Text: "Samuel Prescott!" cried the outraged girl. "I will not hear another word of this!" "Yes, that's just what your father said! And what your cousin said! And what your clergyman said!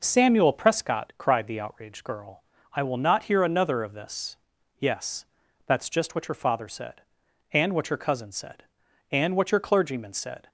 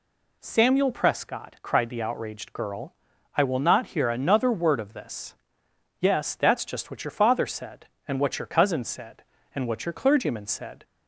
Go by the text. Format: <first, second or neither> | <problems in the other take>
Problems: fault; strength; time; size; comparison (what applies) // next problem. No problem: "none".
second | skips "word"; at 3.8 s